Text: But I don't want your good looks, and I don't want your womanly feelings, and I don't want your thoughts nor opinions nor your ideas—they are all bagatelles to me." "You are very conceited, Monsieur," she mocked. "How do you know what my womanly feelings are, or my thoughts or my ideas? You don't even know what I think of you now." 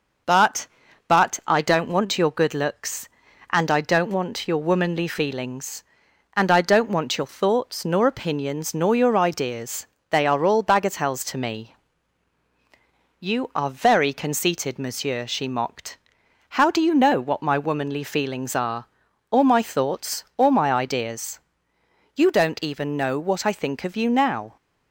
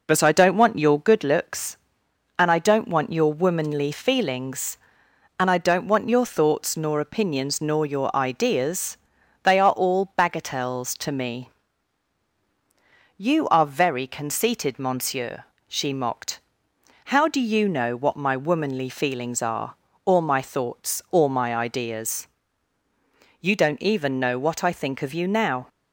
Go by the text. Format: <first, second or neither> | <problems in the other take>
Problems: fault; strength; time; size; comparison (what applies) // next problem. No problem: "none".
second | says "But" twice; at 1.0 s